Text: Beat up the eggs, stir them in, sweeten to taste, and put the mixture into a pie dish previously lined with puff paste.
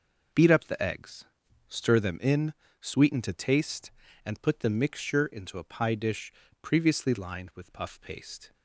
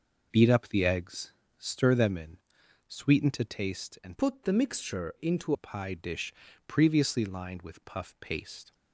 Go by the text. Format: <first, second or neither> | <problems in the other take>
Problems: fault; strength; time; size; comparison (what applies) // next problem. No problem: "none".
first | changes voice from "put" to "into"; from 4.1 to 5.5 s; 1.4 s long // pauses between "dish" and "previously"; slight; at 6.3 s; 0.36 s long; slight in the first